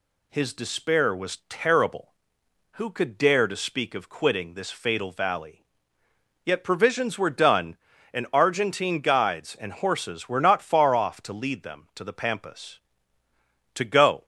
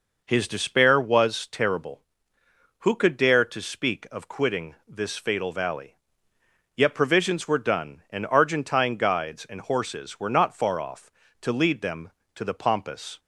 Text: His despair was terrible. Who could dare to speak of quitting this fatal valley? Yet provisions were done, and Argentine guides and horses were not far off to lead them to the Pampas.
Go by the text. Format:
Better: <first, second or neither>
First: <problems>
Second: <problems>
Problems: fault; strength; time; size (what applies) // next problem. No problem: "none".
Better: second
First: goes on to say "To go"; from 13.7 s on; 0.50 s long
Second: none